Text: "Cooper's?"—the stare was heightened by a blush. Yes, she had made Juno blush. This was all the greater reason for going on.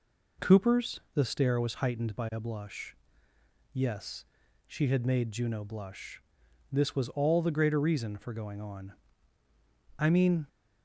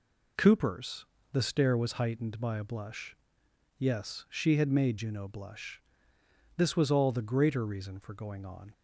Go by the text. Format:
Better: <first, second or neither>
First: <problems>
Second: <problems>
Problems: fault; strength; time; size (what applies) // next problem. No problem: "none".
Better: second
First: goes on to say "I mean"; slight; from 9.9 s on; 0.48 s long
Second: none